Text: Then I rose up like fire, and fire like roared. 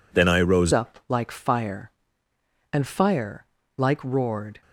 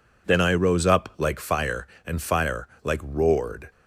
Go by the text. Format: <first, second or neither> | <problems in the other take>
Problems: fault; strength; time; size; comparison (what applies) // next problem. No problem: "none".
second | changes voice at "up"; from 0.7 s on; 3.9 s long // pauses between "fire" and "like"; slight; at 3.4 s; 0.32 s long; slight in the second